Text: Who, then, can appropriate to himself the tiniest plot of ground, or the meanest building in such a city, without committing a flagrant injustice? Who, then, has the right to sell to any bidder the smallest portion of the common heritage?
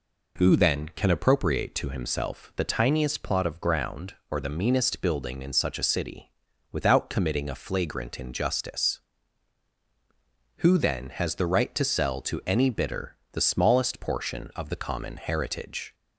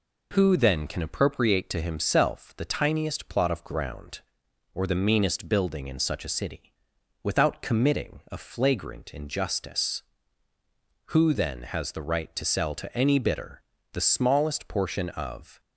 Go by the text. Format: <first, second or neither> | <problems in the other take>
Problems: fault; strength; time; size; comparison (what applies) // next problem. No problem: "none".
first | pauses between "bidder" and "the"; slight; at 13.5 s; 0.32 s long; slight in the first // stops before "the common heritage"; at 15.5 s